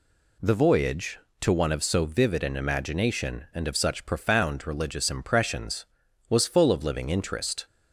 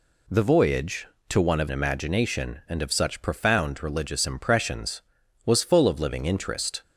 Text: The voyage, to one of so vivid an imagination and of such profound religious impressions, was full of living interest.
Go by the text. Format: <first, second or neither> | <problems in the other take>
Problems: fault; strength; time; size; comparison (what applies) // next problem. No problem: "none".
first | skips "so vivid an"; at 1.6 s